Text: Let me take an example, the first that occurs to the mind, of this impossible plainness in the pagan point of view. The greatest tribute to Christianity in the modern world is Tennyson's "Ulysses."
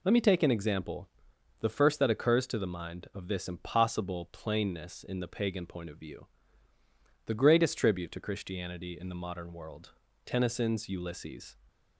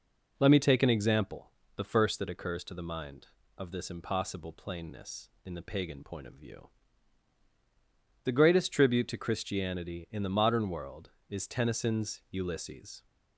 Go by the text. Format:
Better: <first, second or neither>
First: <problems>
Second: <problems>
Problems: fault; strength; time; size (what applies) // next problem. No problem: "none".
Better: second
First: skips "is"; at 10.0 s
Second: none